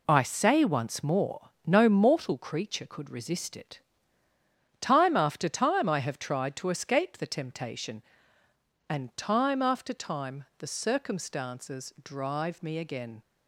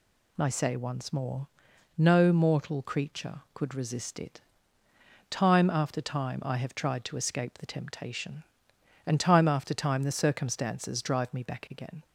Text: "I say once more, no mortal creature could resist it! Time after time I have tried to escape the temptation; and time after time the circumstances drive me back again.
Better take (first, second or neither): second